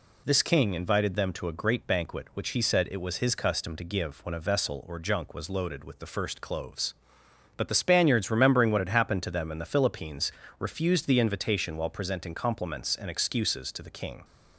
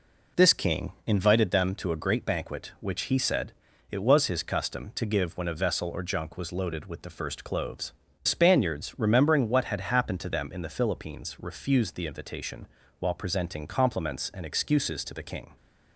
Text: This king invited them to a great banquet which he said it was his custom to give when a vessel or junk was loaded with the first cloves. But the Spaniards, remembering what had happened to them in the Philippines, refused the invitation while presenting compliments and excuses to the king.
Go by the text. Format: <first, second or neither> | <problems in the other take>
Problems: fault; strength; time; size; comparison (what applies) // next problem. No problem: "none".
first | pauses between "said" and "it"; at 3.5 s; 0.40 s long // skips "But the"; at 8.0 s // pauses between "invitation" and "while"; slight; at 12.6 s; 0.32 s long